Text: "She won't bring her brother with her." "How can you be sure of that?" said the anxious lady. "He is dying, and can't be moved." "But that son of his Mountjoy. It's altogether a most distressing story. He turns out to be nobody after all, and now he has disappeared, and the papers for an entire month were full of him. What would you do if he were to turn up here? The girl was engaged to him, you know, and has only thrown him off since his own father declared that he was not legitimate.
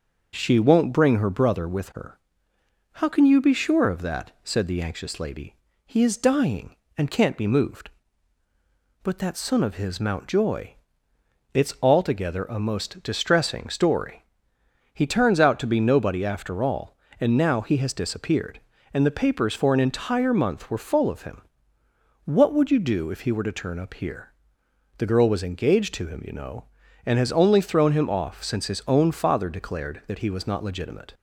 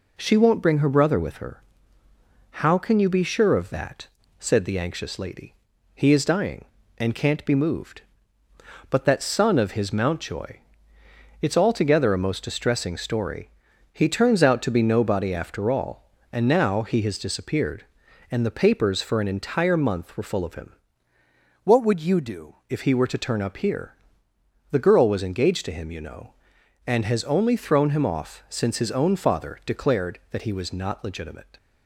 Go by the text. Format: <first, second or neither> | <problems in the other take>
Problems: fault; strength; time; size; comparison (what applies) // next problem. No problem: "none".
first | changes voice from "What" to "do"; from 21.6 to 22.5 s; 0.9 s long